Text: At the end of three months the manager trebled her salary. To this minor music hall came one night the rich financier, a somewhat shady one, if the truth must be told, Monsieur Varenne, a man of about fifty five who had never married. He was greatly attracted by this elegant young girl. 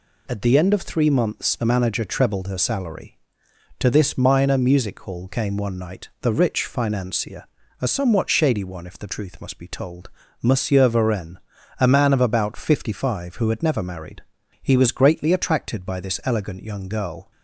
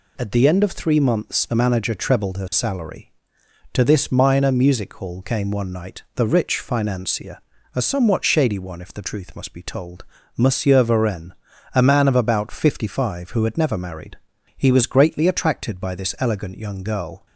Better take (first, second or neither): neither